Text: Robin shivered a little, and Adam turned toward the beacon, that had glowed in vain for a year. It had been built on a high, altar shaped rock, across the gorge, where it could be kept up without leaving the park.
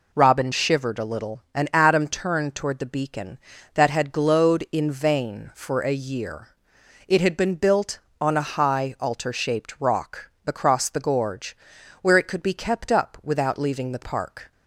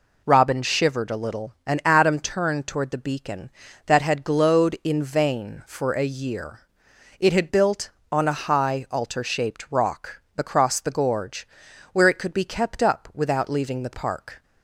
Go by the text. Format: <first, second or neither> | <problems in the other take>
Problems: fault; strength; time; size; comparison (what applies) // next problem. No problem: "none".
first | skips "been"; at 7.4 s